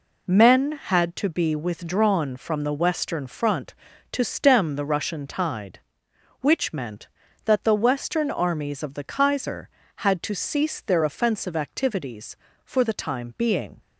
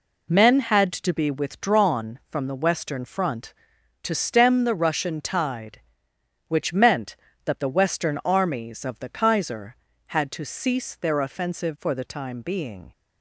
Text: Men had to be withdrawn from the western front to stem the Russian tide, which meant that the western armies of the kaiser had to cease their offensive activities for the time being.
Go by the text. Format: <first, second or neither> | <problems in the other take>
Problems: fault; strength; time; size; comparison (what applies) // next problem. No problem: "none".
first | skips "activities"; at 11.7 s